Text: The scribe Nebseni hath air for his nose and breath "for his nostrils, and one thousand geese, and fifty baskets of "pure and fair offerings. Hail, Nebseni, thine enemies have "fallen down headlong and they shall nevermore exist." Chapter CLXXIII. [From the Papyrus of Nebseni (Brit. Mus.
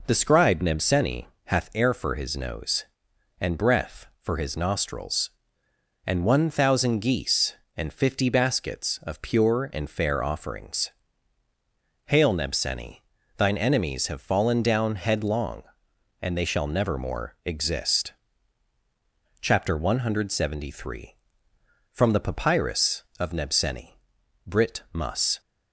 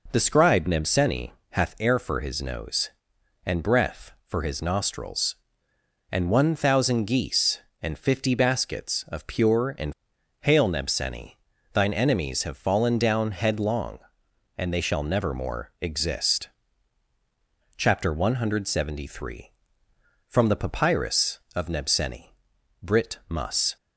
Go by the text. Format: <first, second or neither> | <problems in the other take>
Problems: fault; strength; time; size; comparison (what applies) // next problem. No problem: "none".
first | pauses between "Nebseni" and "hath"; slight; at 1.3 s; 0.18 s long; slight in the first // skips "fair offerings"; at 10.1 s